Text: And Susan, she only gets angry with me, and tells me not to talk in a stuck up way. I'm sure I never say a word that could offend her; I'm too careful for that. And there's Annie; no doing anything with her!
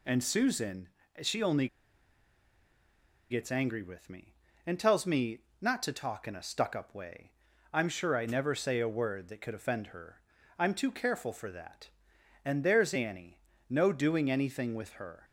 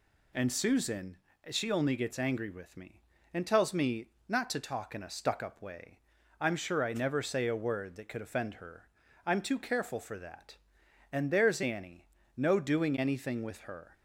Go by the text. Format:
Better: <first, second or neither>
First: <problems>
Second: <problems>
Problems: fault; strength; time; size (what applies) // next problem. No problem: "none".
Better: second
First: pauses between "only" and "gets"; strong; at 1.6 s; 1.6 s long // pauses between "me" and "not"; slight; at 5.3 s; 0.22 s long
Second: pauses between "me" and "not"; slight; at 4.0 s; 0.22 s long